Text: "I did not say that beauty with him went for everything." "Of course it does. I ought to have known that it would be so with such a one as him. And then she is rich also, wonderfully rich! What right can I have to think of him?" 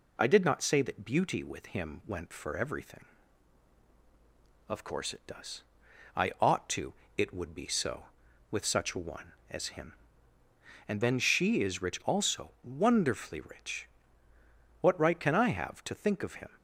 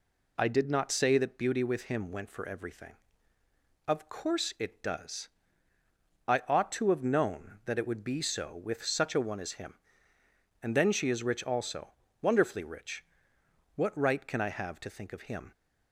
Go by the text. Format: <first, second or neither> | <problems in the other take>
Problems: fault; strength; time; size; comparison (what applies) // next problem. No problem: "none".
second | skips "have known that"; at 7.0 s